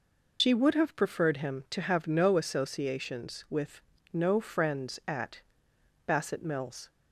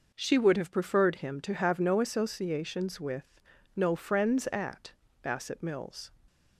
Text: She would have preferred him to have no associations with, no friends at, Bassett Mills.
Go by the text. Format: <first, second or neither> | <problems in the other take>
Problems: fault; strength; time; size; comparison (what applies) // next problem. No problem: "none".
second | loses the start of "She"; at 0.3 s; 70 ms